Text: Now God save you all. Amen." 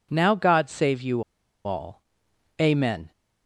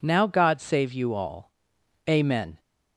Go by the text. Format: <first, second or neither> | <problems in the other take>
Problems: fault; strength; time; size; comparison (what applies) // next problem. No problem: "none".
second | pauses between "you" and "all"; at 1.2 s; 0.43 s long